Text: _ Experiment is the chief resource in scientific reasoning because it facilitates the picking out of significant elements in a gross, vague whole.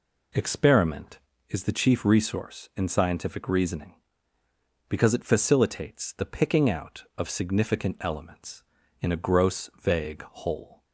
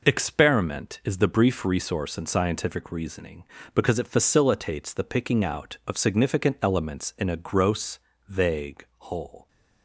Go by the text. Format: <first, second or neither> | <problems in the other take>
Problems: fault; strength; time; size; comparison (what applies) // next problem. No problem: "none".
first | says "brief" for "chief"; at 1.2 s // pauses between "vague" and "whole"; slight; at 8.8 s; 0.15 s long